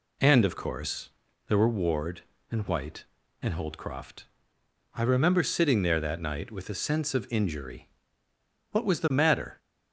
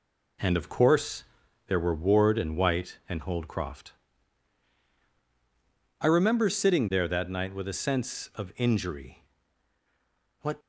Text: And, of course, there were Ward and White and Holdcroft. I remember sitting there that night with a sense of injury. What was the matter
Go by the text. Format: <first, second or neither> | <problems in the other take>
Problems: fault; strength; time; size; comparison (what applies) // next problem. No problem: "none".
first | stops before "was the matter"; at 10.5 s